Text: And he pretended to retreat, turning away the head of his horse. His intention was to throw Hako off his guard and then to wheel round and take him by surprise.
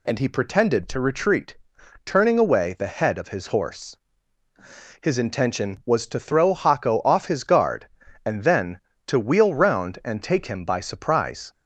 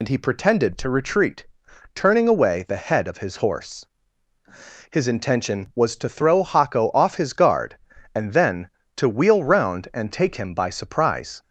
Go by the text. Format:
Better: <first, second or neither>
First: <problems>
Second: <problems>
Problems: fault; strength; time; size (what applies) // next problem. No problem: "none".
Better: first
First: none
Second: loses the start of "And"; at 0.0 s; 60 ms